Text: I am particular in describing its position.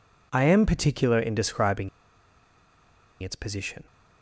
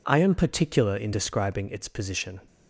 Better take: second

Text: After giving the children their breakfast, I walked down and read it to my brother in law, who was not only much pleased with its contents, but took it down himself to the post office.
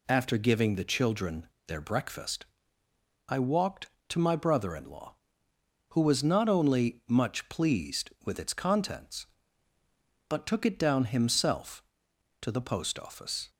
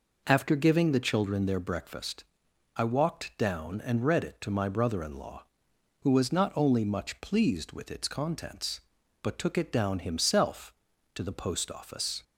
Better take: second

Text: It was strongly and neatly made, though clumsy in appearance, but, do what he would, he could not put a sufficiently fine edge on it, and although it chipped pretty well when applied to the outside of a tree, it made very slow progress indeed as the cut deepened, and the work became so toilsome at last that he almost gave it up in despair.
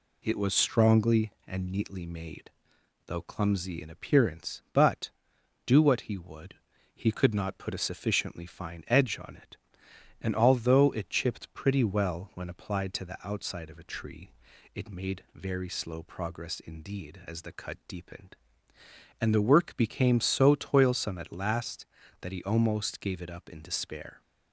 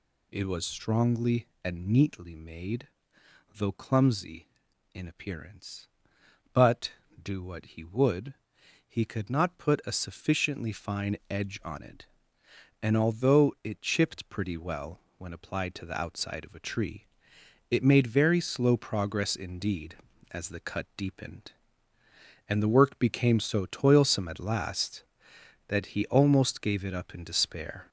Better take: first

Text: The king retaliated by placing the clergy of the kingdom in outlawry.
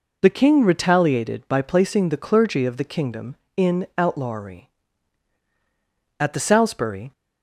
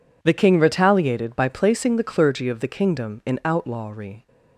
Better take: second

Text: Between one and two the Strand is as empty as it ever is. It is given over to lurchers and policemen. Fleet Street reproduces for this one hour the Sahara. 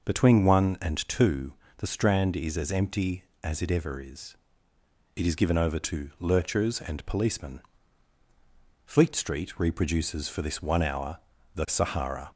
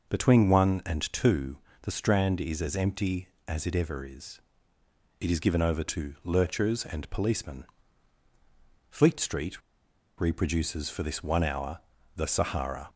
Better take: first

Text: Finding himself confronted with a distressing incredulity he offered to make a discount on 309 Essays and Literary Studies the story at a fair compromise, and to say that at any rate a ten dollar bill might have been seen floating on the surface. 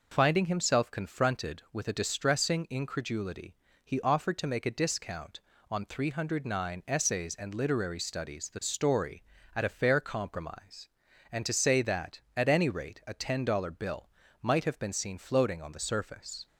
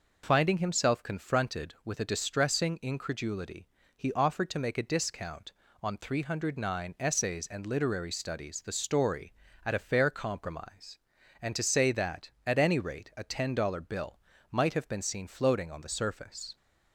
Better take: neither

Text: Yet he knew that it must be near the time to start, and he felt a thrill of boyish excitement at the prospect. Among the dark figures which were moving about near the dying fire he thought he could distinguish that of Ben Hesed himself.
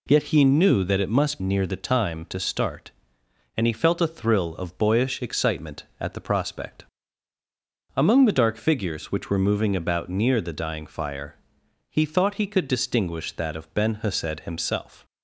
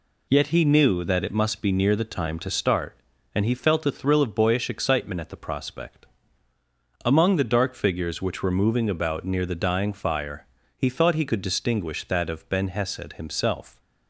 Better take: second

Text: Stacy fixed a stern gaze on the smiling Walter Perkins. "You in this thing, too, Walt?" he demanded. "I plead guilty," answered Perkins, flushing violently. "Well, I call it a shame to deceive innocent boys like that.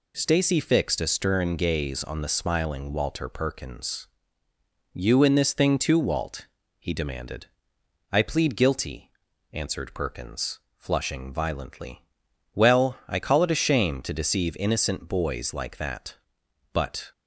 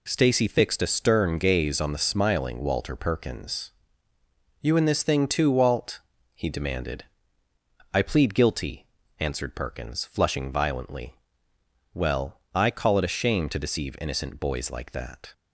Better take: second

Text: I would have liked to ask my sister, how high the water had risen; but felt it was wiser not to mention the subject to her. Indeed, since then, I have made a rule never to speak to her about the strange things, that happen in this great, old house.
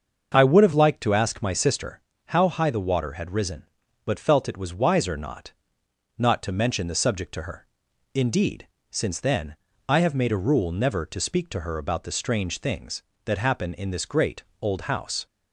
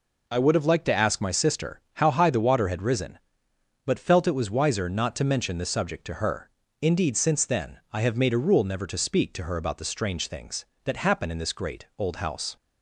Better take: second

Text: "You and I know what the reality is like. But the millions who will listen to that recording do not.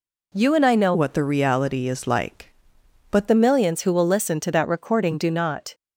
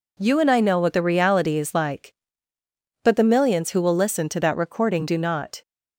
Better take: second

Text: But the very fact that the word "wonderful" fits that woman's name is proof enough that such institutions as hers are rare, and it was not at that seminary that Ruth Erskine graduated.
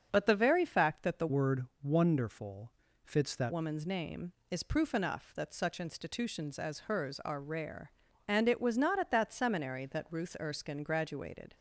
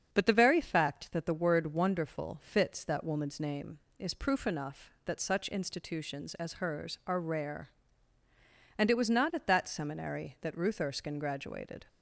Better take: second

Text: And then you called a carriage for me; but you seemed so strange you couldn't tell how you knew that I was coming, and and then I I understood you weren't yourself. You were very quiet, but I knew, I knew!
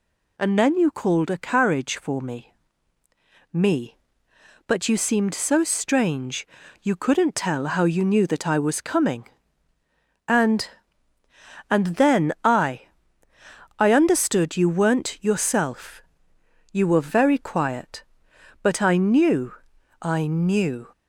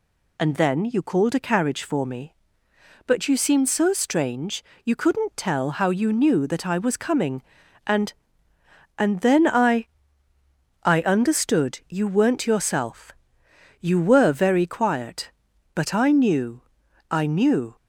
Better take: second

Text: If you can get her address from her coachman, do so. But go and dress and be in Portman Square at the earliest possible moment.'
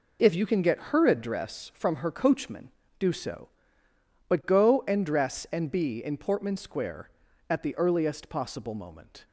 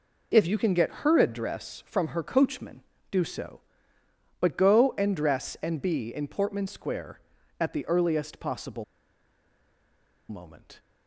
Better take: first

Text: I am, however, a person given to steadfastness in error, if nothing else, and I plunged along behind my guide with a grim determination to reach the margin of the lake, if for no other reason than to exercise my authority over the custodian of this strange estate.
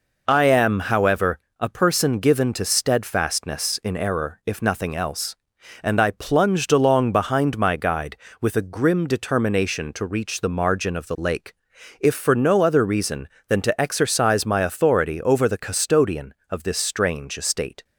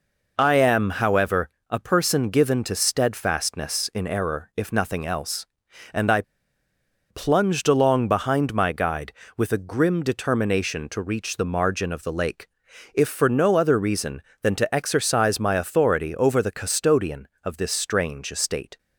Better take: first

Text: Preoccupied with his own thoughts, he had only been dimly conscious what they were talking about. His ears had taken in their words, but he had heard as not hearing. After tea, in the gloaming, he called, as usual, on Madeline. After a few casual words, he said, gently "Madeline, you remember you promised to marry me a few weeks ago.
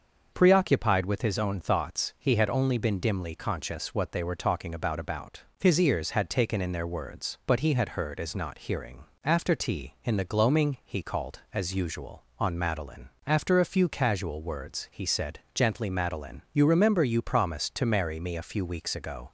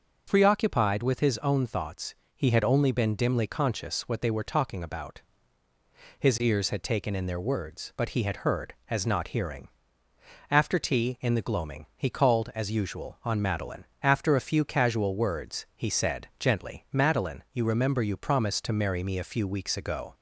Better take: second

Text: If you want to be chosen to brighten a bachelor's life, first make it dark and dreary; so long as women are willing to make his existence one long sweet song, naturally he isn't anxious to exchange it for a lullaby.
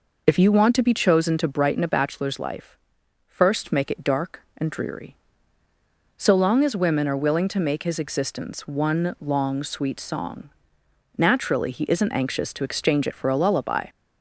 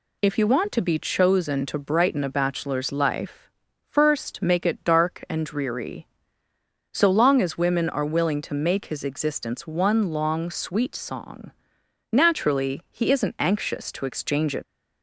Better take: first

